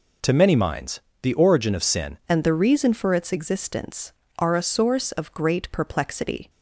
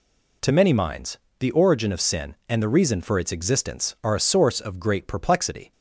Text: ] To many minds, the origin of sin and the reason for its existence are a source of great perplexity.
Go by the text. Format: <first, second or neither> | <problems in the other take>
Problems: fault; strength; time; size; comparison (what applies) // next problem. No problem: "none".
second | changes voice at "and"; from 2.2 s on; 4.2 s long